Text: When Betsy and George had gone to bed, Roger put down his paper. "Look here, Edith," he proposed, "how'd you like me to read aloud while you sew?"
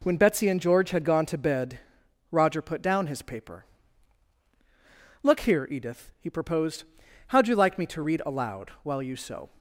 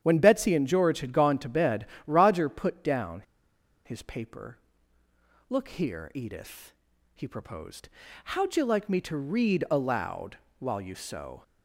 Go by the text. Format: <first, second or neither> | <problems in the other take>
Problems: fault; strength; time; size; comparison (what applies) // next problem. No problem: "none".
first | starts louder than the rest; strong; until 1.0 s; 9.5 dB // pauses between "down" and "his"; noticeable; at 3.2 s; 0.62 s long // pauses between "aloud" and "while"; slight; at 10.3 s; 0.22 s long